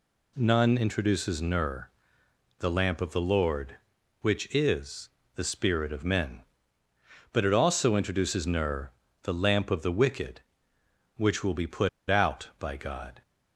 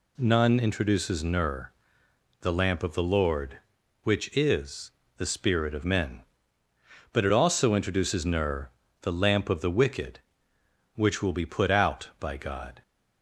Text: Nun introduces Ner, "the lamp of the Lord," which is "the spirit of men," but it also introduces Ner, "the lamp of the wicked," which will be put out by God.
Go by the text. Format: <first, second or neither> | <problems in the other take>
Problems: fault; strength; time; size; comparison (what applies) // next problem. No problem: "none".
second | pauses between "is" and "the"; slight; at 5.0 s; 0.26 s long; slight in the second // pauses between "put" and "out"; slight; at 11.8 s; 0.20 s long